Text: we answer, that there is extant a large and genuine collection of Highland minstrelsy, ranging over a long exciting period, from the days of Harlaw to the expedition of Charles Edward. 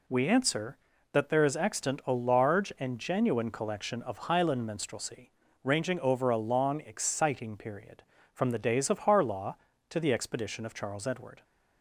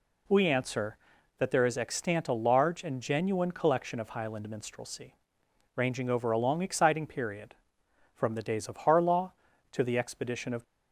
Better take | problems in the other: first | stops before "Charles Edward"; at 10.6 s

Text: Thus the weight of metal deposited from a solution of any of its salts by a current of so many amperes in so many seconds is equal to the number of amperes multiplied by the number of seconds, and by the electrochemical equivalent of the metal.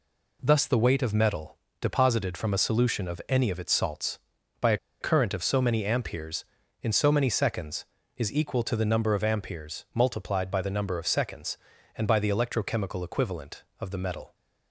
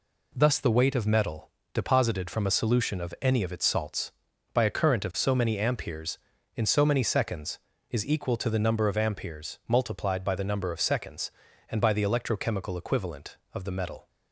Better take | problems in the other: second | pauses between "metal" and "deposited"; slight; at 1.5 s; 0.24 s long; slight in the second // pauses between "a" and "current"; slight; at 4.7 s; 0.24 s long

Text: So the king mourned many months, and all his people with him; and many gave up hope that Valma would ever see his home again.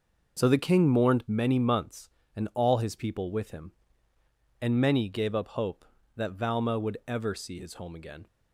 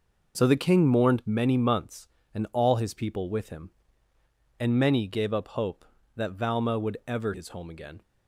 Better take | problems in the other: first | skips "see"; at 7.3 s

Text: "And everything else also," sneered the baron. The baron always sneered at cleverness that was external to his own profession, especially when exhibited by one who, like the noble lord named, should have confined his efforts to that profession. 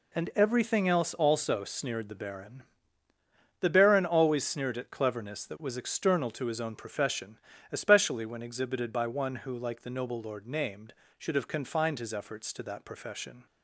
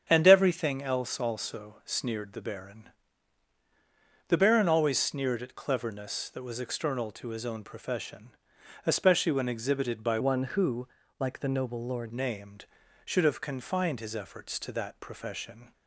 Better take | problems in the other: first | starts louder than the rest; strong; until 1.0 s; 7.5 dB // changes voice from "one" to "lord"; from 10.2 to 12.1 s; 1.9 s long

